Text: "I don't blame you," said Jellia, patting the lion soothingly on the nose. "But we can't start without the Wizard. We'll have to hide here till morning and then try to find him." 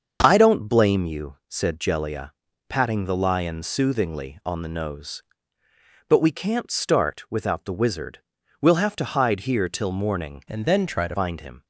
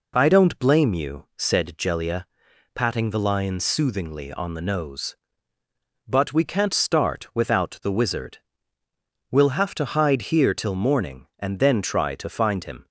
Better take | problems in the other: second | starts louder than the rest; until 1.2 s; 6.5 dB // changes voice from "and" to "to"; from 10.4 to 11.1 s; 0.7 s long

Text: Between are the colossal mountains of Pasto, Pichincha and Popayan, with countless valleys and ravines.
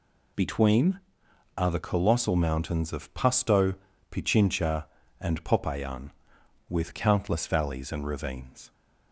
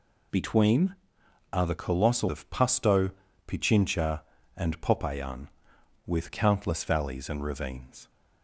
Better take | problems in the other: first | skips "mountains"; at 2.2 s

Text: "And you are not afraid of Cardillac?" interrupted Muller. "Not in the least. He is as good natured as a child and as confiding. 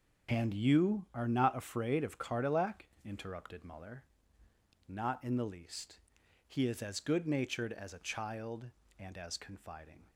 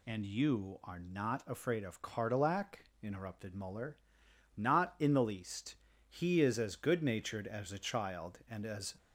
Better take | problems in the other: first | stops before "confiding"; at 8.9 s

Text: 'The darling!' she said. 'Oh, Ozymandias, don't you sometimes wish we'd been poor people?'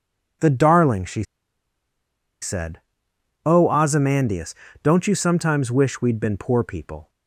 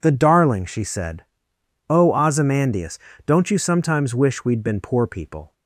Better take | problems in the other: second | pauses between "she" and "said"; at 1.2 s; 1.1 s long

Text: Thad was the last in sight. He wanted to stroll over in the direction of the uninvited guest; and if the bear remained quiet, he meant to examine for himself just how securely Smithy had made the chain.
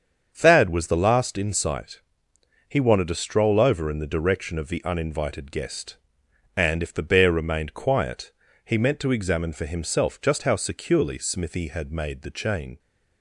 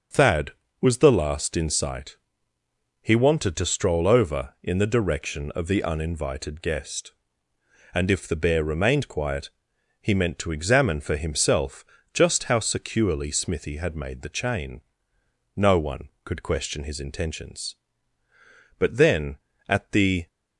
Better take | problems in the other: first | starts louder than the rest; strong; until 1.4 s; 7 dB; strong in the first // pauses between "himself" and "just"; slight; at 11.8 s; 0.30 s long // goes on to say "No one could question his intentions but then at the"; strong; from 15.5 s on; 4.7 s long

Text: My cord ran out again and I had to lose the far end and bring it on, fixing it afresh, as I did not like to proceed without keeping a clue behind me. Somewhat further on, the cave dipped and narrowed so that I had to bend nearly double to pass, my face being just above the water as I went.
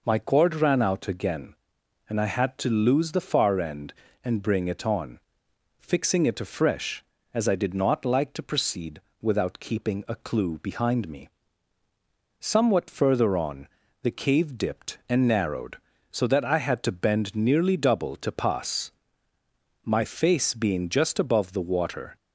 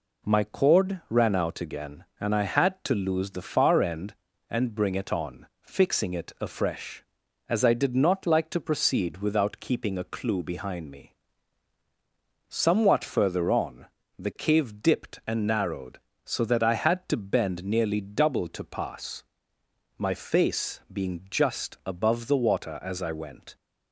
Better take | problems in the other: second | pauses between "proceed" and "without"; slight; at 8.9 s; 0.22 s long // stops before "as I went"; at 22.1 s

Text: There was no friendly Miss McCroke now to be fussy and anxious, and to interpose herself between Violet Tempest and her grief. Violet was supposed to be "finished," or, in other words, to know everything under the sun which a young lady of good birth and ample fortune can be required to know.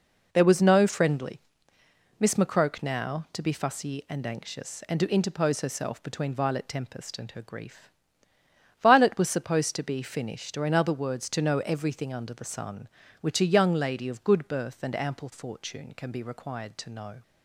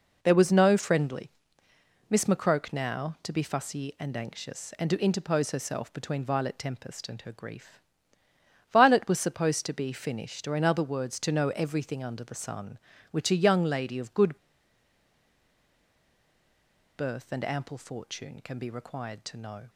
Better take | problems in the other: first | pauses between "friendly" and "Miss"; noticeable; at 1.3 s; 0.80 s long; noticeable in the first // pauses between "good" and "birth"; strong; at 14.3 s; 2.6 s long

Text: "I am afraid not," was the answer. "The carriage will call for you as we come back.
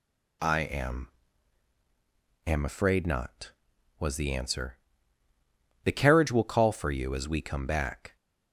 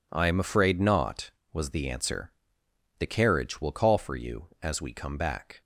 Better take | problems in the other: second | says "am" twice; at 2.4 s

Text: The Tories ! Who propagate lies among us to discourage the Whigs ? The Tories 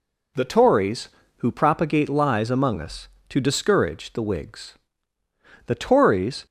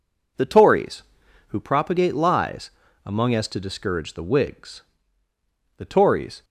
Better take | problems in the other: first | pauses between "lies" and "among"; slight; at 2.7 s; 0.34 s long // says "as" for "us"; at 3.3 s

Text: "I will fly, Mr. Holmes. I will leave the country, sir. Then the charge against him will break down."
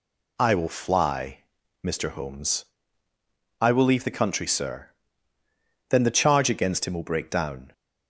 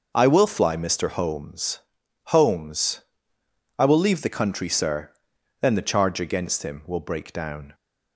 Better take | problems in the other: first | says "Holmes" twice; at 2.2 s

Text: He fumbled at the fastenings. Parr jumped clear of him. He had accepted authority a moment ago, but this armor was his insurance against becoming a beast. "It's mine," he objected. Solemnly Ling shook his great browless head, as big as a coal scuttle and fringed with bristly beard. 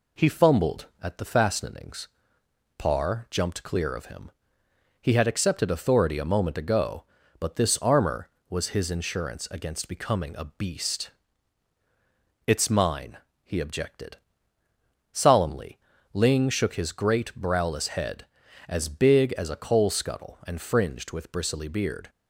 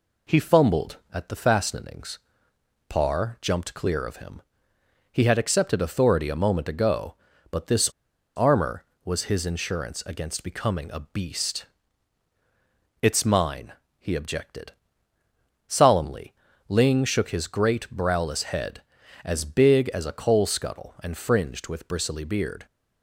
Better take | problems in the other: first | pauses between "this" and "armor"; noticeable; at 7.8 s; 0.48 s long // pauses between "Solemnly" and "Ling"; at 16.3 s; 0.38 s long; also in the first

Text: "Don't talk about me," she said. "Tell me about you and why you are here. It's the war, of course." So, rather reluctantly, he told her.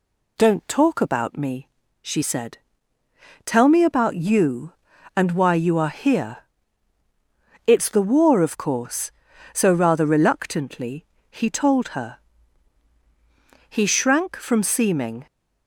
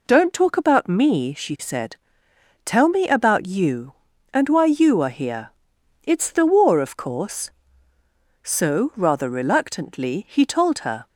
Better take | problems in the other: second | goes on to say "He shrank from seeming"; from 13.6 s on; 1.5 s long

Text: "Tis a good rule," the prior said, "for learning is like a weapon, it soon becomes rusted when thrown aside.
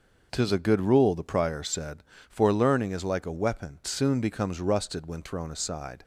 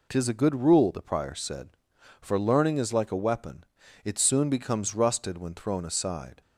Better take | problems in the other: second | skips "it"; at 3.8 s

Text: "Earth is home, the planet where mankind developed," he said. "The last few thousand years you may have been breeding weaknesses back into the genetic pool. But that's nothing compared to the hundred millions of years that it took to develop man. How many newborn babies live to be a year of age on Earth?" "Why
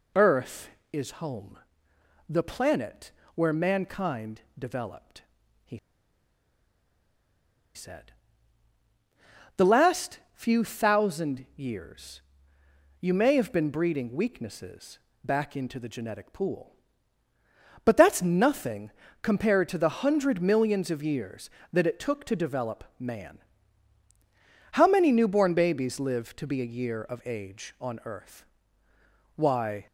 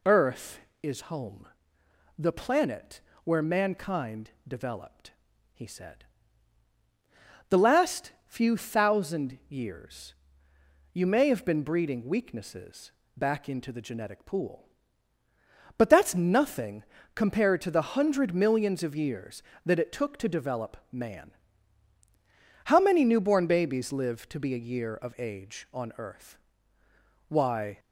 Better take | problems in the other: second | pauses between "planet" and "where"; slight; at 3.1 s; 0.22 s long; slight in the second // pauses between "mankind" and "developed"; slight; at 4.4 s; 0.18 s long; slight in the second // pauses between "he" and "said"; strong; at 5.7 s; 1.9 s long // pauses between "years" and "you"; noticeable; at 12.2 s; 0.80 s long; noticeable in the second // pauses between "weaknesses" and "back"; slight; at 14.9 s; 0.26 s long; slight in the second // pauses between "nothing" and "compared"; slight; at 18.9 s; 0.32 s long; slight in the second

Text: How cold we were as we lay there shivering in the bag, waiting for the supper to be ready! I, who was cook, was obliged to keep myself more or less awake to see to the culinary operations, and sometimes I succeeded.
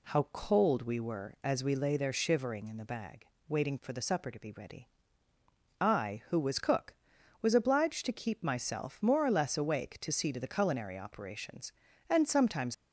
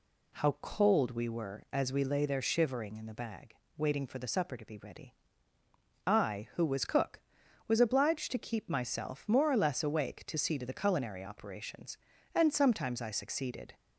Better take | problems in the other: second | stops before "I succeeded"; at 12.7 s

